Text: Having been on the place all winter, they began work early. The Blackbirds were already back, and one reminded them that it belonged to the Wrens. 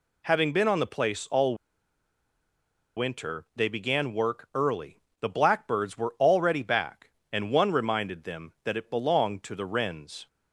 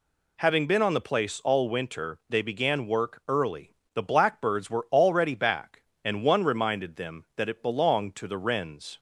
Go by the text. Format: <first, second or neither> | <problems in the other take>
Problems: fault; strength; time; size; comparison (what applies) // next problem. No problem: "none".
second | pauses between "all" and "winter"; strong; at 1.5 s; 1.4 s long